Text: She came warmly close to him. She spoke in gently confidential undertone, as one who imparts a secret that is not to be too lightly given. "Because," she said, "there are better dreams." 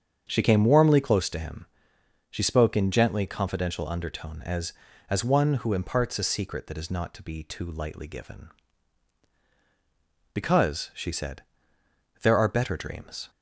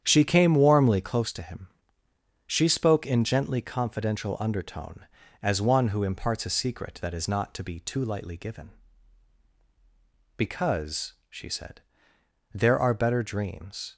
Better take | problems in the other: second | starts louder than the rest; strong; until 1.2 s; 7.5 dB; strong in the second // says "as" twice; at 5.0 s

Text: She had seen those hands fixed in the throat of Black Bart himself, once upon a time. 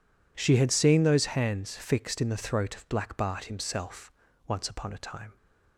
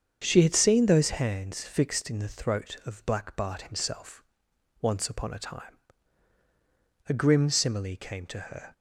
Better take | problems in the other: first | starts louder than the rest; strong; until 1.2 s; 7.5 dB // goes on to say "A grim simile came to her"; from 7.0 s on; 1.6 s long

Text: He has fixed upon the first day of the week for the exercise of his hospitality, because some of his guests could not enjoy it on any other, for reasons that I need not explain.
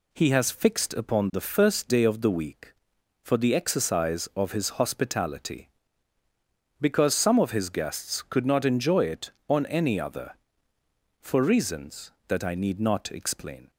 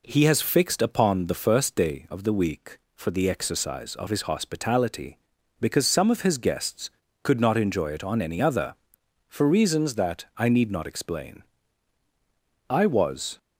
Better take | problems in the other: first | goes on to say "I was"; noticeable; from 12.6 s on; 0.70 s long

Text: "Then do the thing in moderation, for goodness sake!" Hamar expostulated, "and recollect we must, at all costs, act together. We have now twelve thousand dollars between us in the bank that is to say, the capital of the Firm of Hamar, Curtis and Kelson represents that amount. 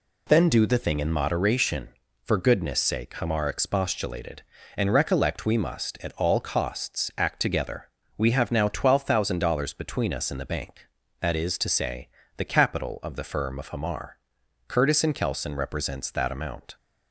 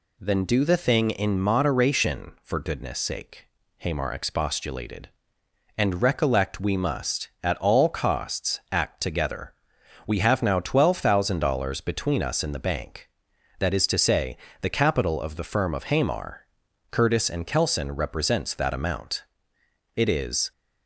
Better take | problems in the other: first | goes on to say "It is"; from 19.9 s on; 0.56 s long

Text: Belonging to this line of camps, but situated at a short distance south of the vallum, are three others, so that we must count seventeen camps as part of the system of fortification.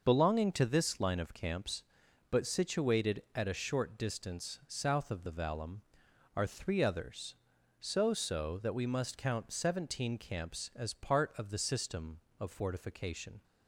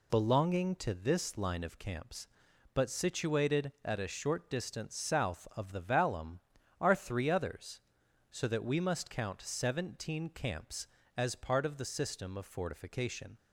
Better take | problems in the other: second | says "so" twice; at 8.1 s

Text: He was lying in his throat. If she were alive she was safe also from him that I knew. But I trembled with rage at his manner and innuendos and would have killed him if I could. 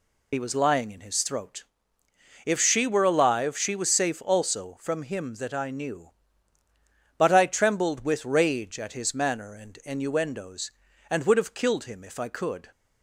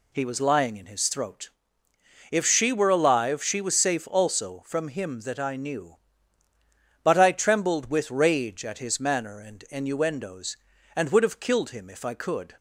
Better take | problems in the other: second | loses the start of "He"; at 0.3 s; 50 ms

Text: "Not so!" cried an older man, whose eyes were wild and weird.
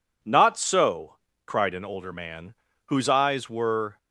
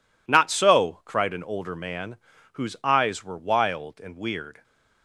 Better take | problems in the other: second | stops before "wild and weird"; at 3.9 s

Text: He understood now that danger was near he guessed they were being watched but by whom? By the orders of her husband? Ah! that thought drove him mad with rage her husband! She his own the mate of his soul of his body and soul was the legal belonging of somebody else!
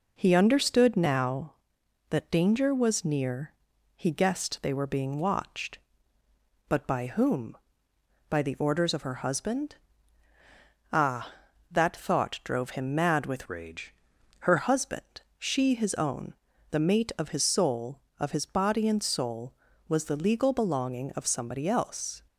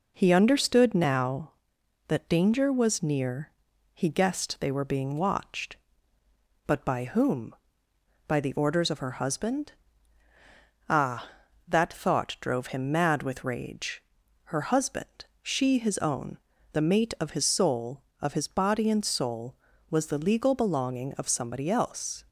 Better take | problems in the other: second | pauses between "near" and "he"; at 3.5 s; 0.42 s long; also in the second // changes voice from "rage" to "her"; from 13.4 to 14.5 s; 1.1 s long // pauses between "rage" and "her"; noticeable; at 13.9 s; 0.46 s long; also in the second // pauses between "own" and "the"; at 16.3 s; 0.38 s long; slight in the second

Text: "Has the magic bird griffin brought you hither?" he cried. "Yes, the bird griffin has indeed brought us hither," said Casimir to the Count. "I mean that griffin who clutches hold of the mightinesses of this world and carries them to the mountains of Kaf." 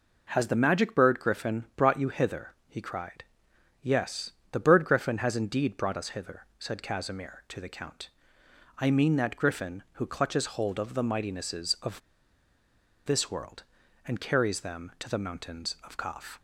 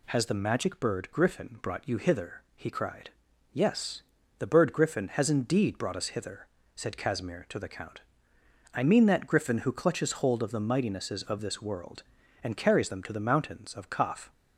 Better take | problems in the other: second | pauses between "of" and "this"; at 11.9 s; 1.0 s long

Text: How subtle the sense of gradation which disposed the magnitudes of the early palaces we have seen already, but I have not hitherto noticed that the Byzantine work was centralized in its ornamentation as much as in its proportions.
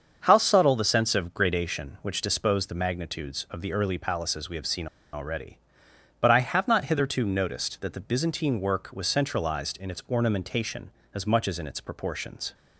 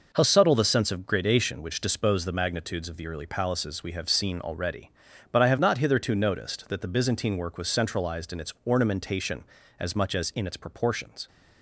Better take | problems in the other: second | starts louder than the rest; until 1.2 s; 7 dB // pauses between "seen" and "already"; slight; at 4.8 s; 0.26 s long

